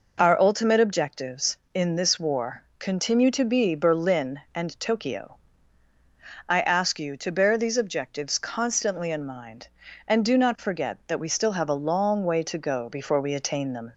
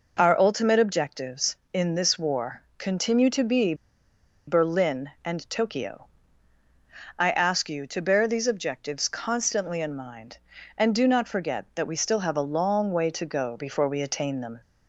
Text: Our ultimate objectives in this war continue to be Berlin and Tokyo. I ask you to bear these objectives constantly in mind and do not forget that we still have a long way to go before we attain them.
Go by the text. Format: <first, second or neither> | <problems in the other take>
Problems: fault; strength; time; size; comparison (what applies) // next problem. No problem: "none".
first | pauses between "war" and "continue"; slight; at 2.6 s; 0.18 s long; slight in the first // pauses between "be" and "Berlin"; noticeable; at 3.7 s; 0.73 s long